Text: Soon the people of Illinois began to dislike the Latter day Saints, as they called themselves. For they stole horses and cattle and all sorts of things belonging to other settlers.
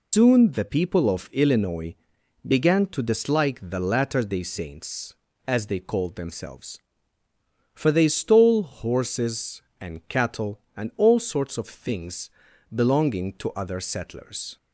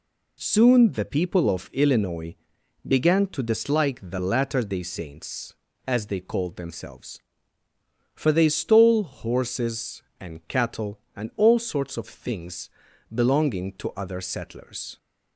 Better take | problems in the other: second | loses the start of "Soon"; at 0.1 s; 130 ms // pauses between "Illinois" and "began"; noticeable; at 1.9 s; 0.50 s long; noticeable in the second // pauses between "things" and "belonging"; at 12.2 s; 0.42 s long; also in the second

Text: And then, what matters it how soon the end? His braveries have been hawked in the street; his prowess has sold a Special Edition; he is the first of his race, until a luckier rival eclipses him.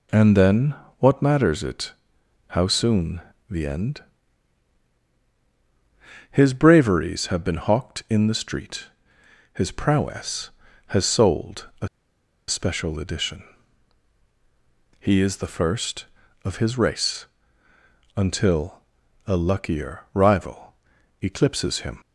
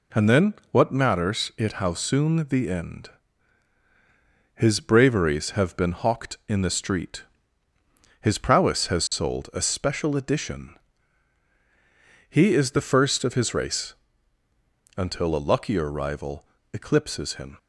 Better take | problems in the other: second | pauses between "it" and "how"; noticeable; at 1.9 s; 0.56 s long // pauses between "soon" and "the"; slight; at 3.2 s; 0.28 s long // pauses between "a" and "Special"; noticeable; at 11.8 s; 0.61 s long // pauses between "until" and "a"; at 18.8 s; 0.44 s long // pauses between "rival" and "eclipses"; noticeable; at 20.7 s; 0.48 s long; slight in the second

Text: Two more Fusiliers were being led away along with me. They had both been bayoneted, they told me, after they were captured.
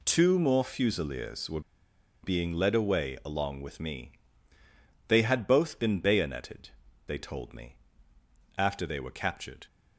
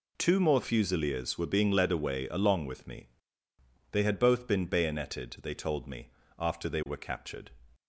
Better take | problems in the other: second | pauses between "were" and "being"; noticeable; at 1.5 s; 0.63 s long

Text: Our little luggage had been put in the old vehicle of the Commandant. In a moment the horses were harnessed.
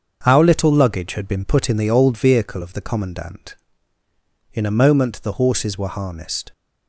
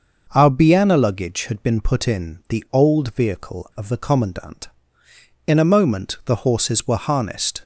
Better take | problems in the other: first | starts louder than the rest; noticeable; until 1.3 s; 6 dB; also in the first // says "biana" for "little"; at 0.5 s

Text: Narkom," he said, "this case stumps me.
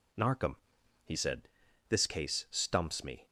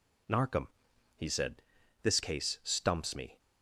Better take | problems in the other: neither | none

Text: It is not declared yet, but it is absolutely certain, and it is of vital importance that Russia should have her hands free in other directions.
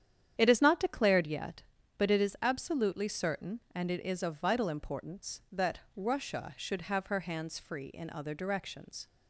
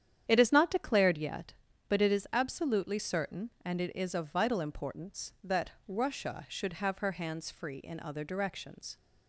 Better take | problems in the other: neither | starts louder than the rest; strong; the same in both // pauses between "that" and "Russia"; slight; the same in both

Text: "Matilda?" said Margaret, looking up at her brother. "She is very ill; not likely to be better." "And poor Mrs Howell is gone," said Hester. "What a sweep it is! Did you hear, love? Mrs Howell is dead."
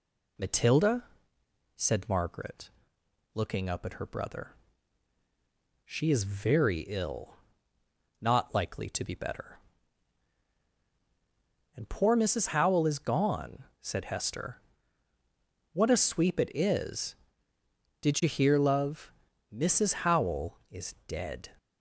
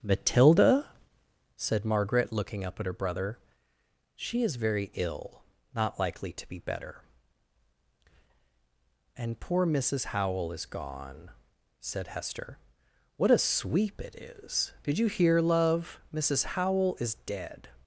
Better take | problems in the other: first | starts louder than the rest; strong; until 1.7 s; 9 dB

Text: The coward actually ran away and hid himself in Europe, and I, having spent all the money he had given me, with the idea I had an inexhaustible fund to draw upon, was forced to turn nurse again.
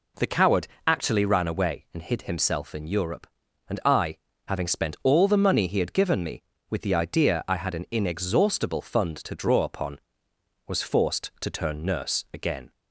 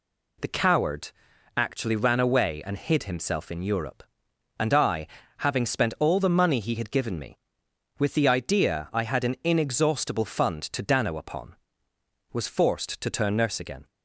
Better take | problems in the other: first | pauses between "coward" and "actually"; noticeable; at 1.1 s; 0.46 s long; slight in the first // says "dano" for "draw"; at 10.8 s

